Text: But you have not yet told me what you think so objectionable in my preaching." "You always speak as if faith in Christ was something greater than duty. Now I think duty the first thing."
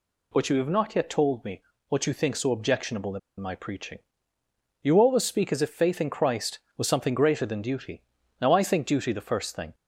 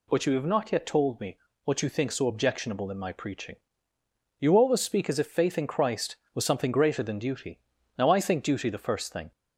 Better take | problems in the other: second | pauses between "me" and "what"; slight; at 1.6 s; 0.28 s long; slight in the second // pauses between "in" and "my"; slight; at 3.1 s; 0.20 s long

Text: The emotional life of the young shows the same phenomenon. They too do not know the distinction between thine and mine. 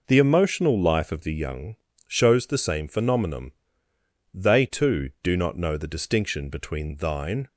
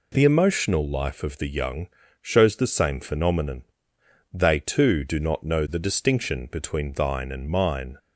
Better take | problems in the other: second | pauses between "young" and "shows"; slight; at 1.7 s; 0.30 s long; slight in the second // stops before "and mine"; at 7.4 s

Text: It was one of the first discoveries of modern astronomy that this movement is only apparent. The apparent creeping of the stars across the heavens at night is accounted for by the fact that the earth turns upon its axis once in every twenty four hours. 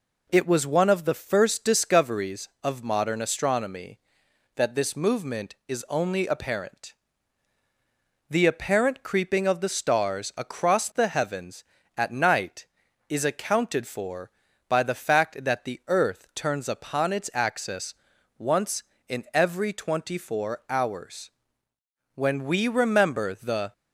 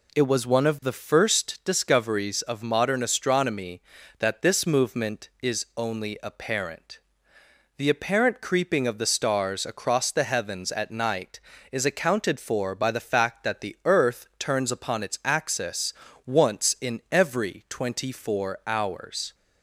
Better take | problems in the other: second | pauses between "axis" and "once"; at 17.9 s; 0.44 s long; slight in the second // goes on to say "When we remember the"; from 22.1 s on; 1.5 s long

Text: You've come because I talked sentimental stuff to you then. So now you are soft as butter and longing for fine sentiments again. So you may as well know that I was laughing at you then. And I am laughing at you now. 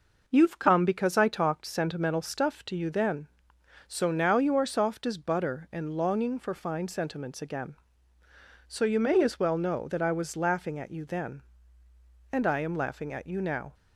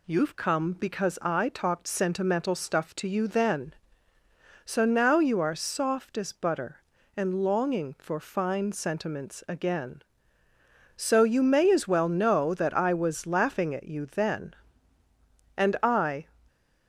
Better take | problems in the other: first | stops before "am laughing at you now"; at 16.4 s

